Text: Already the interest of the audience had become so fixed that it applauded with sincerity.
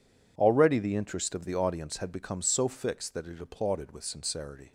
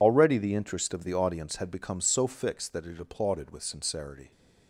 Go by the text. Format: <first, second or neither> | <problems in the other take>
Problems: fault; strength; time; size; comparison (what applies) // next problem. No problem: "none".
first | loses the start of "Already"; at 0.0 s; 45 ms